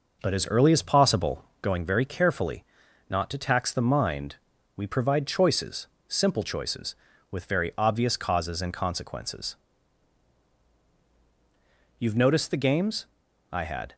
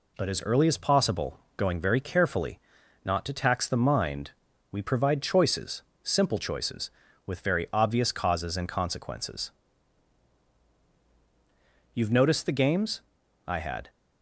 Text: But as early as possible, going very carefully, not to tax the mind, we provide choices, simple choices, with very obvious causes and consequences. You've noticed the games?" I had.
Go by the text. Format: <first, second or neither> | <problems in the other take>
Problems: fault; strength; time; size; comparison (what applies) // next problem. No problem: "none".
second | starts louder than the rest; noticeable; until 1.5 s; 5.5 dB